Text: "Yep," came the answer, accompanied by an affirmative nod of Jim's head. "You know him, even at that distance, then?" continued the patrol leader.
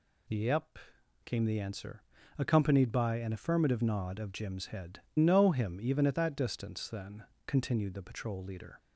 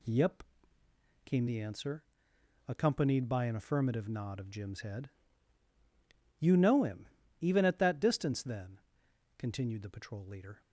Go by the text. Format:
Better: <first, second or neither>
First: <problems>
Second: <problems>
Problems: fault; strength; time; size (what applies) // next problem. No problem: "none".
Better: second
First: skips "You"; at 5.0 s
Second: none